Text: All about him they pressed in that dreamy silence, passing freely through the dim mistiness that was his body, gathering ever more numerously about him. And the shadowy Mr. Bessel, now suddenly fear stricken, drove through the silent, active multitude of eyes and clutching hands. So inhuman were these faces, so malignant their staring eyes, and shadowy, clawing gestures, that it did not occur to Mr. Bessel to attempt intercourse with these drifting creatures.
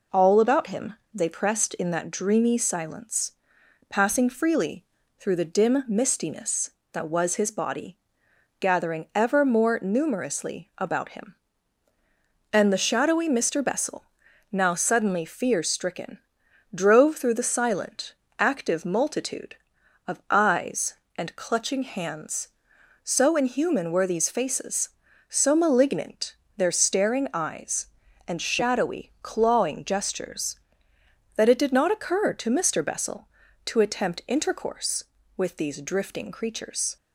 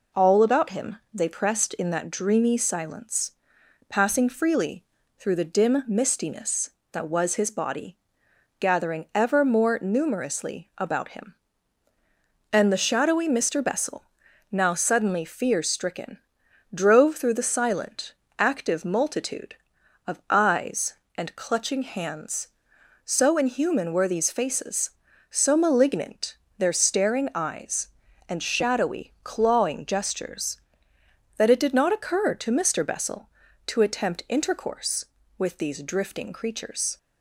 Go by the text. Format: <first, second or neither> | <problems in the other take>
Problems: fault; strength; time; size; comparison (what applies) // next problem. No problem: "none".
neither | pauses between "him" and "they"; slight; the same in both // pauses between "freely" and "through"; slight; the same in both // pauses between "malignant" and "their"; slight; the same in both